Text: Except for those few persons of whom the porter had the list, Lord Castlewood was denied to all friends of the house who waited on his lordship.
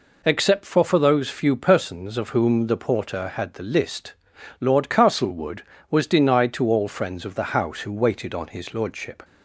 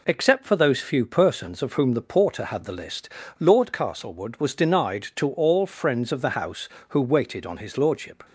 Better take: second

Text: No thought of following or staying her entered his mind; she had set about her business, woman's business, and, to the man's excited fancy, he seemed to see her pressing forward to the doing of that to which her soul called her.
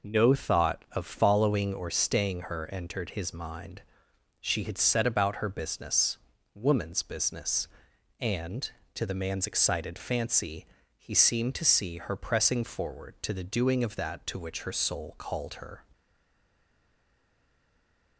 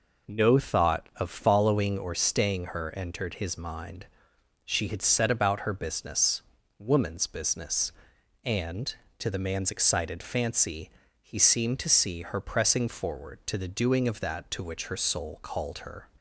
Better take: second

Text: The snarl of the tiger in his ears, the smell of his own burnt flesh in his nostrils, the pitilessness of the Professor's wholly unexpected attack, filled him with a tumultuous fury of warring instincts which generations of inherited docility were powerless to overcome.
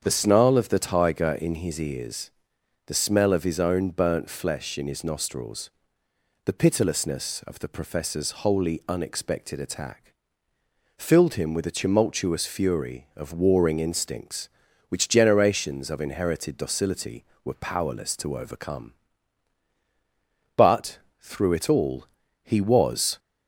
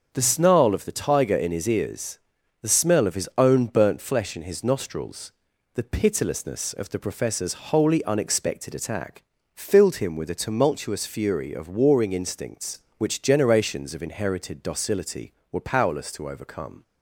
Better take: second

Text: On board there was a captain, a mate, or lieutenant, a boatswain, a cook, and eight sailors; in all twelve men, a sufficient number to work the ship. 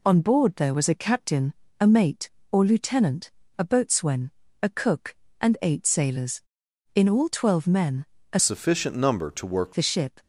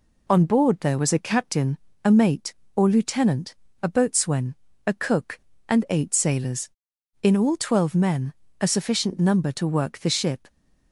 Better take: second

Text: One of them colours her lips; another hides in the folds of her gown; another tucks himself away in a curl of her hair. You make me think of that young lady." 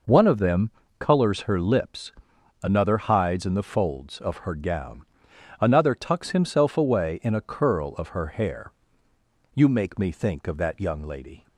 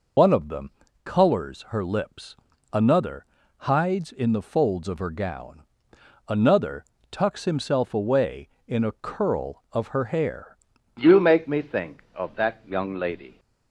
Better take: first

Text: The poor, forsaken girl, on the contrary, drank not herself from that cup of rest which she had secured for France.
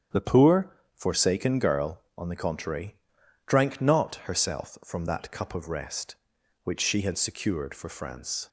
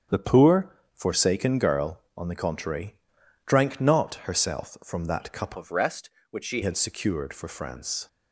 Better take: first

